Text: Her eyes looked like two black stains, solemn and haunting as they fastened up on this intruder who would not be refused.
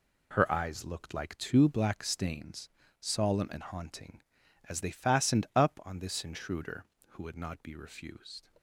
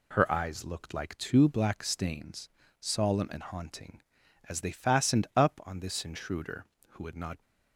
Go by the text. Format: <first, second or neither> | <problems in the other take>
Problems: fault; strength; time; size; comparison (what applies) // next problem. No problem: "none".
first | stops before "be refused"; at 7.4 s